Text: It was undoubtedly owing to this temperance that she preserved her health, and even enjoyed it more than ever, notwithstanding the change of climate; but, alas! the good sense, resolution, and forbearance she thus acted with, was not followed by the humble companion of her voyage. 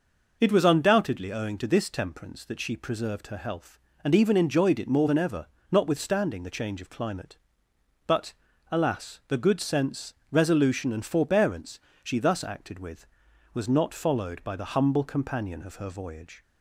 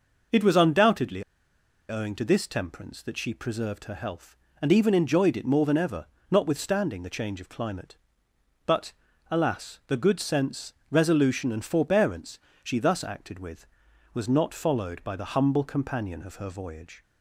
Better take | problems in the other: first | pauses between "undoubtedly" and "owing"; noticeable; at 1.2 s; 0.66 s long // pauses between "forbearance" and "she"; slight; at 12.3 s; 0.24 s long; slight in the first

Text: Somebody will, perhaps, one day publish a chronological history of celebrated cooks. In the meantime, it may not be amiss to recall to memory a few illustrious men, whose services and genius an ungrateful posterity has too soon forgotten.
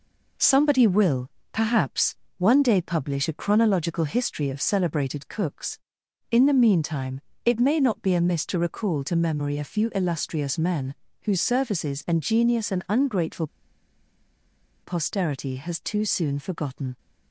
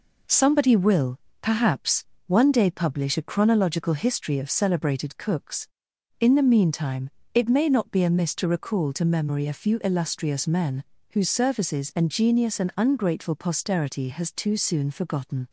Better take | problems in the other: second | pauses between "ungrateful" and "posterity"; strong; at 13.4 s; 1.3 s long

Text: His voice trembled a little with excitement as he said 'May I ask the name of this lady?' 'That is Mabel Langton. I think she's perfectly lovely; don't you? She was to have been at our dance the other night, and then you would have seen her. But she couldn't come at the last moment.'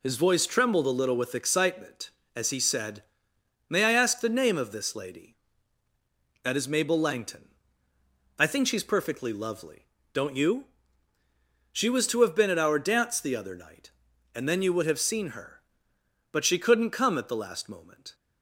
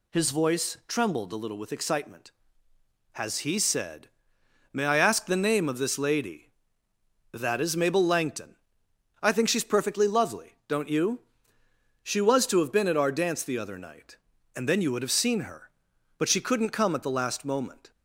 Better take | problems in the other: first | says "has" for "as"; at 3.1 s // pauses between "said" and "May"; noticeable; at 4.0 s; 0.64 s long; noticeable in the first

